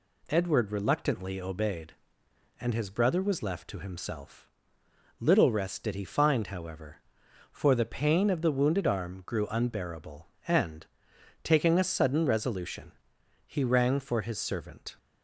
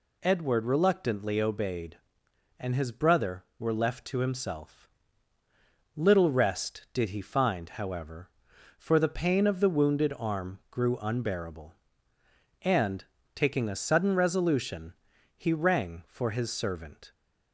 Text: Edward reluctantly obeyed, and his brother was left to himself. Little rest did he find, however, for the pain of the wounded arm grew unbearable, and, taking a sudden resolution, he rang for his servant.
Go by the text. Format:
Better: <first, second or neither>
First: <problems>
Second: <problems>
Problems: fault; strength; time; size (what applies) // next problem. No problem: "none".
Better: first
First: none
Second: says "were" for "was"; at 3.5 s